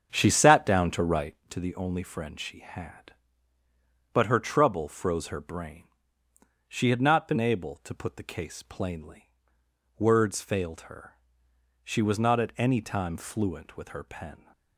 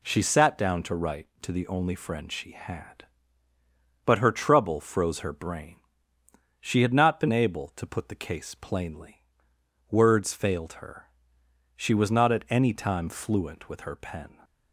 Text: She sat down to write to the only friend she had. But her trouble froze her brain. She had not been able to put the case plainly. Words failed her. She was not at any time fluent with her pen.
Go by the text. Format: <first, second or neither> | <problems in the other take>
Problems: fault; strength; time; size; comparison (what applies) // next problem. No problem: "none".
second | starts louder than the rest; strong; until 1.6 s; 7.5 dB